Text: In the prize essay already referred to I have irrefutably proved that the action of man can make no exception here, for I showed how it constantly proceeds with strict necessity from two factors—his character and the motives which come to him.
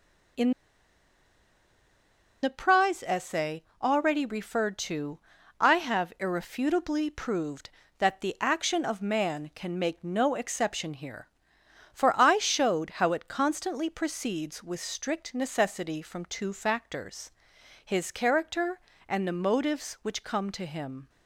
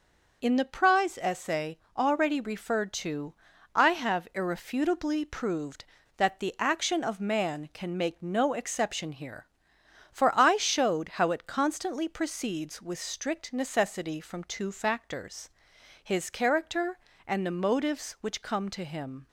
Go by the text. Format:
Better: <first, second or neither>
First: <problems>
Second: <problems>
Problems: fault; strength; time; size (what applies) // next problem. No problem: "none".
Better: second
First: pauses between "In" and "the"; strong; at 0.5 s; 1.8 s long // pauses between "essay" and "already"; slight; at 3.6 s; 0.18 s long // pauses between "to" and "I"; at 5.1 s; 0.40 s long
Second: pauses between "essay" and "already"; slight; at 1.7 s; 0.18 s long // pauses between "to" and "I"; at 3.3 s; 0.40 s long